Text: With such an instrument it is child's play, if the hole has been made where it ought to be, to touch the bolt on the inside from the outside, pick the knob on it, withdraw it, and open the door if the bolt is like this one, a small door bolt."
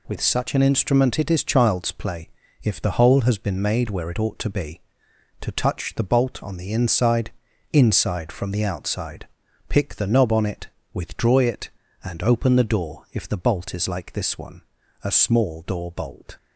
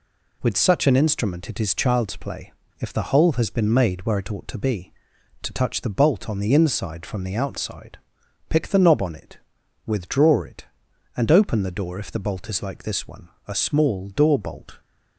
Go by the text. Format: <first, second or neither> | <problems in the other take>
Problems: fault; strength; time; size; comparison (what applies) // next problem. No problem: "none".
second | says "inside" twice; at 7.7 s